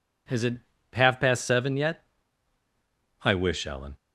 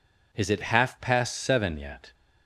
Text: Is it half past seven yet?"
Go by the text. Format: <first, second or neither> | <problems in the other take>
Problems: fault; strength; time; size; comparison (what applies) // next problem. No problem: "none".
second | pauses between "it" and "half"; slight; at 0.5 s; 0.36 s long // goes on to say "I wish Ellen"; noticeable; from 3.2 s on; 0.74 s long